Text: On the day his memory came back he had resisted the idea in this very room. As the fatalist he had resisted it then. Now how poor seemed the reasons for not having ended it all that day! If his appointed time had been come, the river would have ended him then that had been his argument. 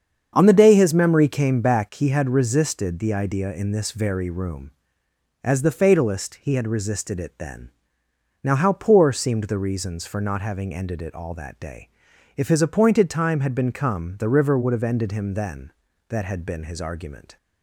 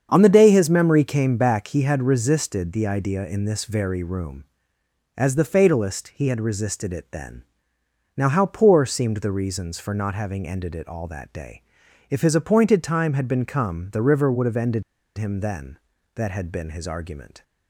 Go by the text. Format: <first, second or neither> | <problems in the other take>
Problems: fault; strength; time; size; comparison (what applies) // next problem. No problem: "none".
first | starts louder than the rest; strong; until 1.1 s; 7.5 dB; strong in the first // pauses between "ended" and "him"; slight; at 14.8 s; 0.34 s long